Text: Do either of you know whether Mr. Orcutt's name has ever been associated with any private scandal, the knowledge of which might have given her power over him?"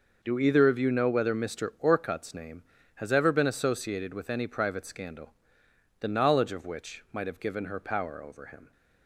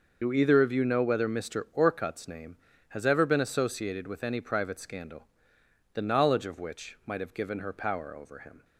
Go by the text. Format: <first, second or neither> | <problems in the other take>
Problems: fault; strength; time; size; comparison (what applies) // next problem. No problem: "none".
first | loses the start of "Do"; at 0.2 s; 40 ms